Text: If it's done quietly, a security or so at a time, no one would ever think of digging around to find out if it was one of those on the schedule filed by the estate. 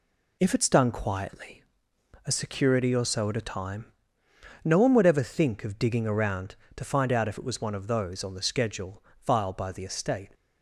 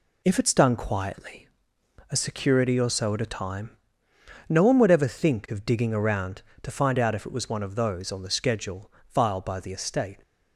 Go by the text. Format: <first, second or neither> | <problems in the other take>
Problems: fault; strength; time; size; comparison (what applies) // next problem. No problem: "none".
neither | pauses between "schedule" and "filed"; slight; the same in both